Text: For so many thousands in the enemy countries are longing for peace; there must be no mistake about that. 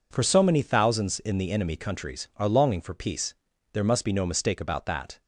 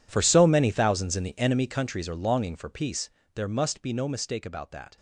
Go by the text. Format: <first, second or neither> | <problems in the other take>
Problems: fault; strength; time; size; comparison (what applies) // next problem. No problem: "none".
first | gets quieter; strong; throughout; 17.5 dB